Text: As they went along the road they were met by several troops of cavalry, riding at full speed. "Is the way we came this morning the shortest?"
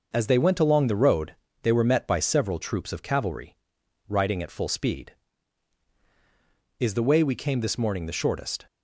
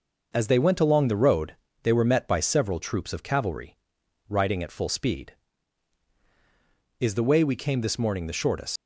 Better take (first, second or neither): first